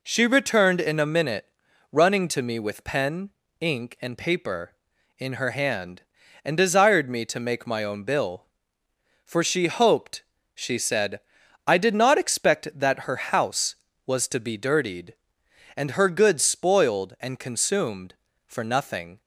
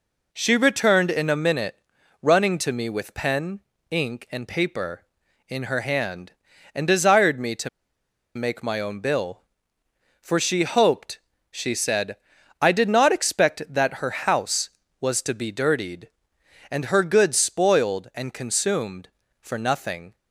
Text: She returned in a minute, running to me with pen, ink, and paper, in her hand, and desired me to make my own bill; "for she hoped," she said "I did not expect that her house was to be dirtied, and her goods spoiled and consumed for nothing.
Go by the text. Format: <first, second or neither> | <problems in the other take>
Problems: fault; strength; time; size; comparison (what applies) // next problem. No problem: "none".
first | pauses between "to" and "make"; noticeable; at 7.6 s; 0.67 s long // pauses between "said" and "I"; at 12.1 s; 0.44 s long; noticeable in the first